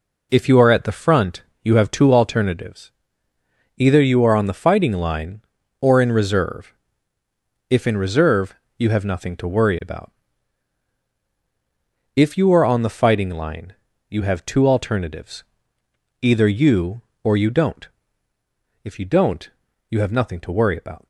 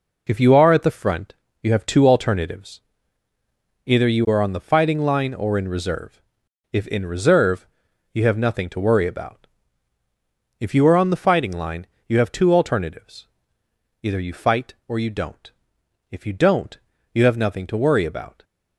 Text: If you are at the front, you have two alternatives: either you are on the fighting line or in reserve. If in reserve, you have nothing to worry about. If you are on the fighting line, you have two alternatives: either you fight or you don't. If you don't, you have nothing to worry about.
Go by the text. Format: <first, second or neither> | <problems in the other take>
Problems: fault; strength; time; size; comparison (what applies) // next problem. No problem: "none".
second | skips "fight"; at 17.1 s